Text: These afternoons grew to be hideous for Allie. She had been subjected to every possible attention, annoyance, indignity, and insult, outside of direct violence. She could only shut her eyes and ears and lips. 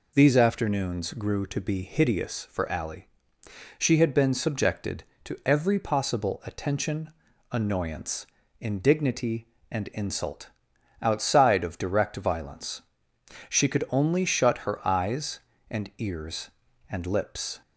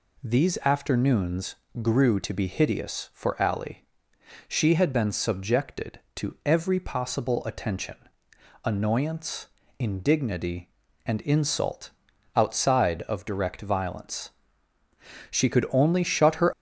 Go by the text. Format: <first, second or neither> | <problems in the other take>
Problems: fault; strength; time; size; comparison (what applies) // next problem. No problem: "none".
first | pauses between "afternoons" and "grew"; slight; at 1.5 s; 0.26 s long // stops before "eyes and ears and lips"; at 16.5 s